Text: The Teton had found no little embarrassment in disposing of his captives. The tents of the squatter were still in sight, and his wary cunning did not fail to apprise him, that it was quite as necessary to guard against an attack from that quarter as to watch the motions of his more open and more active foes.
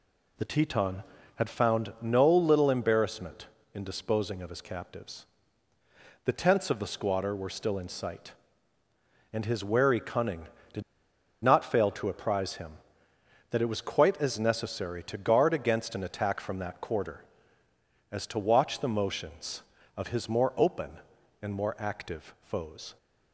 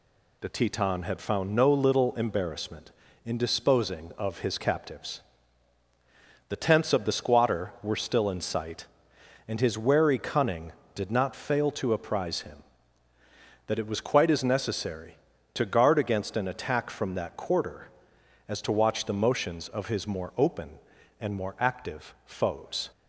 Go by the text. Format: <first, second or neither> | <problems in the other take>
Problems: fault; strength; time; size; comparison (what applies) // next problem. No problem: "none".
second | pauses between "did" and "not"; noticeable; at 10.8 s; 0.59 s long